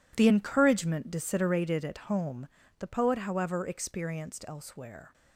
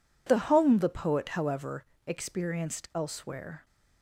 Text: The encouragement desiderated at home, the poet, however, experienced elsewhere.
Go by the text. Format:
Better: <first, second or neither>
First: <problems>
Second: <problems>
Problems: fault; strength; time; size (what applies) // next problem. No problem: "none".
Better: first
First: none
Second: skips "encouragement desiderated at"; at 0.4 s